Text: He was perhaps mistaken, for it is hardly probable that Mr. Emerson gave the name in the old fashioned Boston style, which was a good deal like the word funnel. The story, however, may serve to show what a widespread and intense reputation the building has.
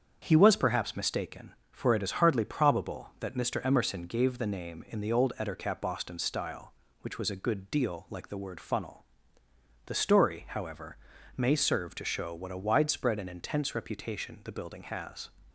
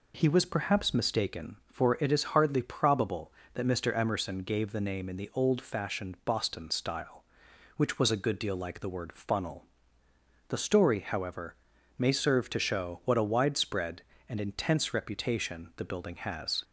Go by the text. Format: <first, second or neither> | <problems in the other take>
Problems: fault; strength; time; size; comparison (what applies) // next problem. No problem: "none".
second | starts louder than the rest; strong; until 1.2 s; 7.5 dB // says "ettercap" for "fashioned"; at 5.3 s